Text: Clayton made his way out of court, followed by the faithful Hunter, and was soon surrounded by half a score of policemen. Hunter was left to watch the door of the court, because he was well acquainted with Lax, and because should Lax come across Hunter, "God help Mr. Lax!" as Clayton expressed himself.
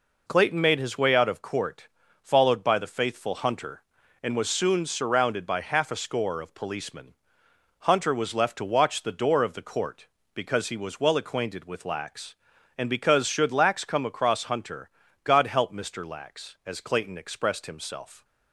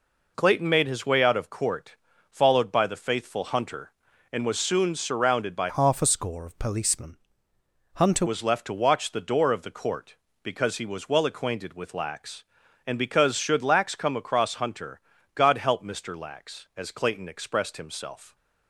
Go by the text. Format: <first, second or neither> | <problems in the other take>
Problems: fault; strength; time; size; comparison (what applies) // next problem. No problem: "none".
first | changes voice from "half" to "Hunter"; from 5.6 to 8.2 s; 2.6 s long